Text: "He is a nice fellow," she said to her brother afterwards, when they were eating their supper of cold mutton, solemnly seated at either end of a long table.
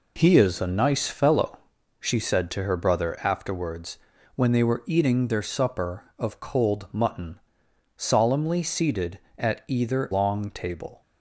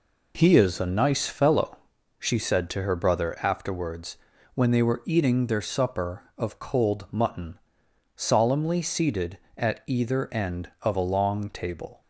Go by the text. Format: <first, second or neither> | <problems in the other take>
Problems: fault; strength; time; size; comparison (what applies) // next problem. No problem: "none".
second | skips "end of a"; at 10.1 s